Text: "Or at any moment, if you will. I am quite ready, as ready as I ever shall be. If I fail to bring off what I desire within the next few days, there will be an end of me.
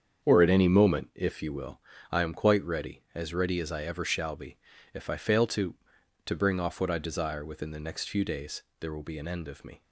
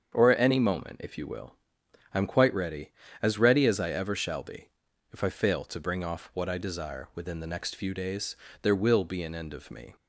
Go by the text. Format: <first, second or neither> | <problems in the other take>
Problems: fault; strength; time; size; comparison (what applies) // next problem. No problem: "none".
second | starts louder than the rest; strong; until 1.2 s; 7.5 dB; strong in the second // says "to" twice; at 6.2 s